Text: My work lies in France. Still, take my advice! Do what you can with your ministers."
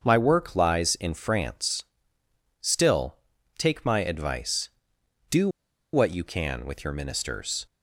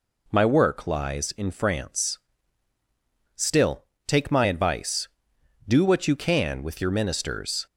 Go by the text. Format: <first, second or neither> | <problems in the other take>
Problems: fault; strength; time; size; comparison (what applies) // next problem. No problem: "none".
second | starts louder than the rest; until 1.0 s; 6.5 dB // pauses between "Do" and "what"; at 5.4 s; 0.45 s long